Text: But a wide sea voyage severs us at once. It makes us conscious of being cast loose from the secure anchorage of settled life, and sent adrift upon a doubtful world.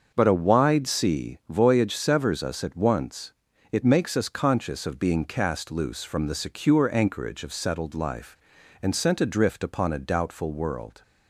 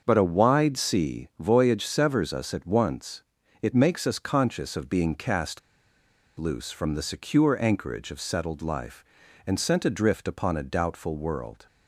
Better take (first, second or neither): first